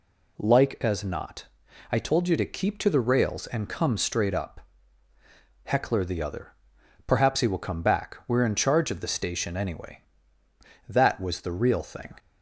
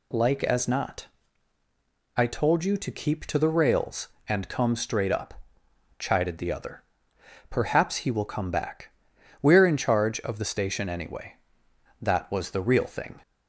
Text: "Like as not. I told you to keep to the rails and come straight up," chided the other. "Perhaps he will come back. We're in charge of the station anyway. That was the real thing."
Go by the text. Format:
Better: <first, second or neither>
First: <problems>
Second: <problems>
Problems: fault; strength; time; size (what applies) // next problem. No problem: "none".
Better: second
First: says "heckler" for "chided"; at 5.6 s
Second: none